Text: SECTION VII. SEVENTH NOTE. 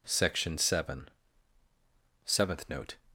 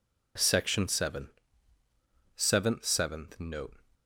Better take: first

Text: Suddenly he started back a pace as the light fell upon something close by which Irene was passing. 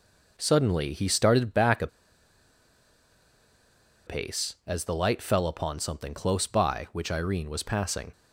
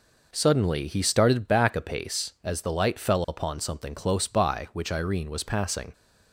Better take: second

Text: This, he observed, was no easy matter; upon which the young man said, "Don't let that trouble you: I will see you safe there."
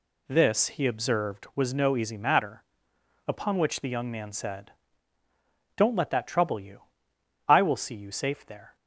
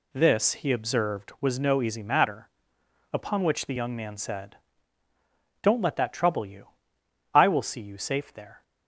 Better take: neither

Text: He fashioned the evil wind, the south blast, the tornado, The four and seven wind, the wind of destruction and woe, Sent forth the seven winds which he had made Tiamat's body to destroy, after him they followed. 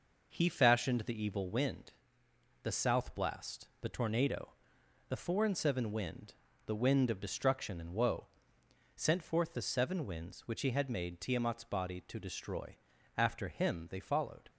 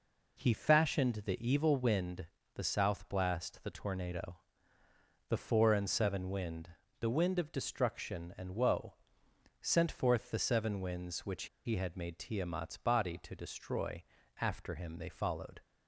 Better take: first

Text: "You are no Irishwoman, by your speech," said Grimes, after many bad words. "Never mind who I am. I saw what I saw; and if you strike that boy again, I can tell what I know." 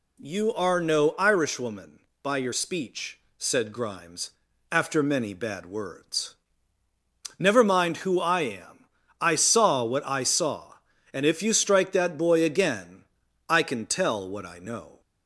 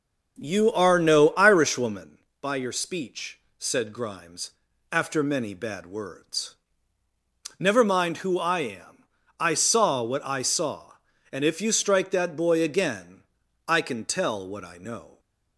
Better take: first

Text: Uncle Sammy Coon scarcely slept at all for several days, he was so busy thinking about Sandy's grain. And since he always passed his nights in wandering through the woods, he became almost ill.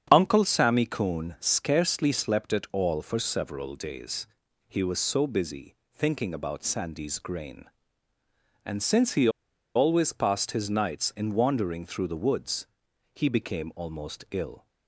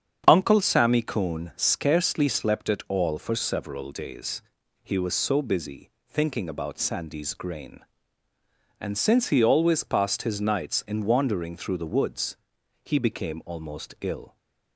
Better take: second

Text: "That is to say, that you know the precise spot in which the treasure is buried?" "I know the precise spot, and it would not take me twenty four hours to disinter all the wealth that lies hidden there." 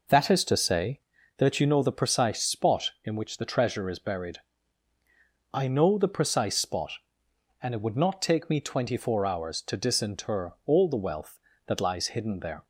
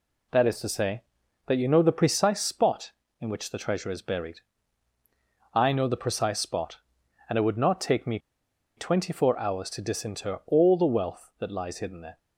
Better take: first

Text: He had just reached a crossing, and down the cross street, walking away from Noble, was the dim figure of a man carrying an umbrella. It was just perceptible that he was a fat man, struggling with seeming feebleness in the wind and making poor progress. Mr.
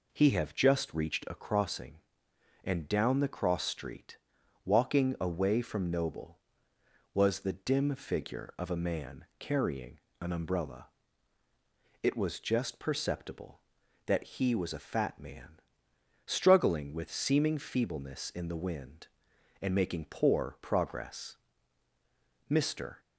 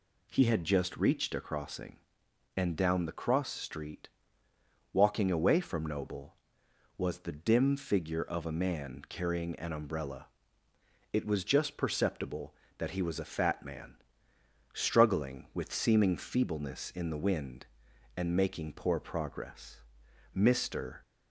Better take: second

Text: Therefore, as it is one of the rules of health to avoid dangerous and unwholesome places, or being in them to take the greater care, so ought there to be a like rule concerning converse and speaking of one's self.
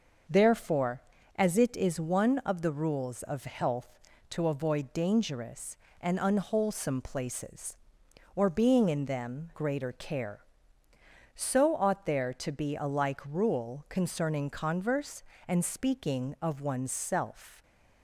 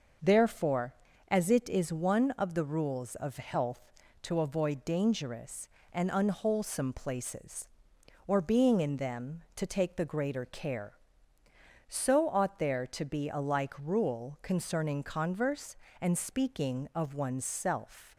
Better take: second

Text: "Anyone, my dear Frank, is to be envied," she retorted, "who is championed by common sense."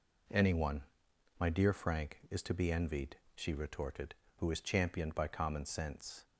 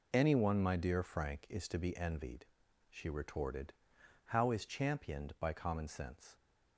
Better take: first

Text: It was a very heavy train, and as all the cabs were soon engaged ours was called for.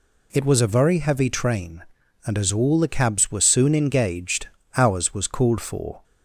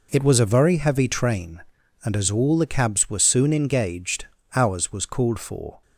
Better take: first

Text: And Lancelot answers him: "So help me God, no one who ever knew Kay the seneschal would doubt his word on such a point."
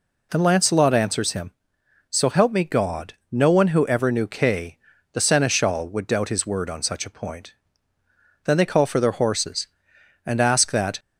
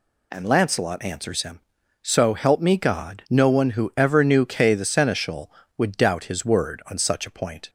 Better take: second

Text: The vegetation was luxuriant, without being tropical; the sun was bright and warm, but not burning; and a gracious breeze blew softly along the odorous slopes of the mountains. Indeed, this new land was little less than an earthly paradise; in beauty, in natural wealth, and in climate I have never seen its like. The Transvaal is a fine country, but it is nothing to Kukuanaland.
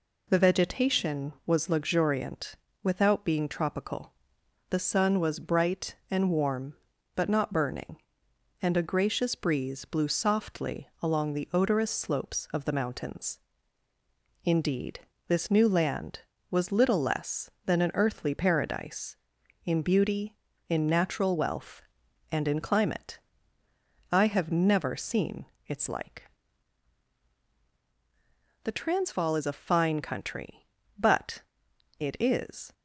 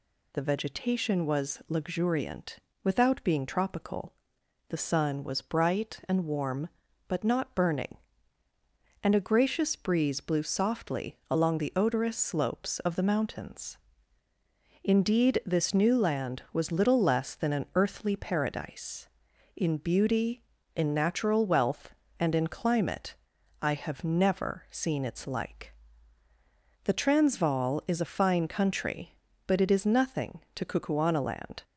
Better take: second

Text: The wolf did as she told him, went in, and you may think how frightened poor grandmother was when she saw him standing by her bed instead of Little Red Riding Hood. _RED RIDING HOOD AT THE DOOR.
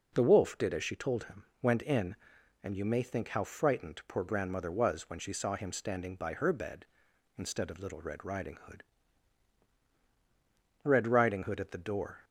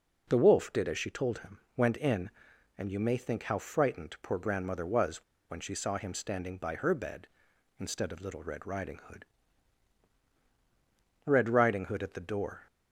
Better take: first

